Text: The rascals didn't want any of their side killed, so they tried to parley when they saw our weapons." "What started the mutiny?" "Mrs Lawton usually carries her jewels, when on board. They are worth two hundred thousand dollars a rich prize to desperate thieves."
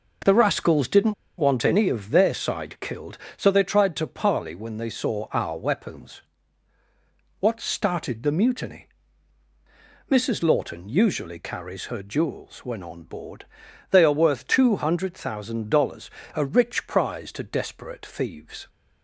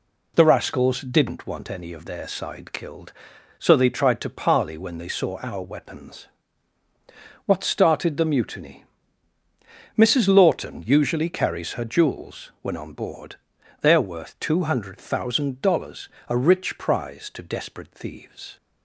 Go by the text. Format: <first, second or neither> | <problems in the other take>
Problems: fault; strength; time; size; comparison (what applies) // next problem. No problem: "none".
second | pauses between "didn't" and "want"; slight; at 1.1 s; 0.26 s long // pauses between "dollars" and "a"; slight; at 16.0 s; 0.28 s long; slight in the second